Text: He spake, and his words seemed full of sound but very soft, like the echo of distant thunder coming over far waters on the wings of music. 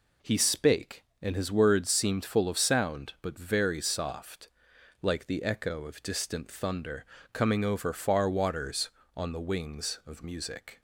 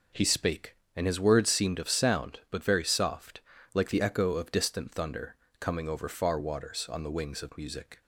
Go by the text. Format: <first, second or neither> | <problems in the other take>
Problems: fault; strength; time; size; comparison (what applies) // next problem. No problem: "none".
first | skips "full"; at 1.7 s // pauses between "thunder" and "coming"; slight; at 5.3 s; 0.24 s long; slight in the first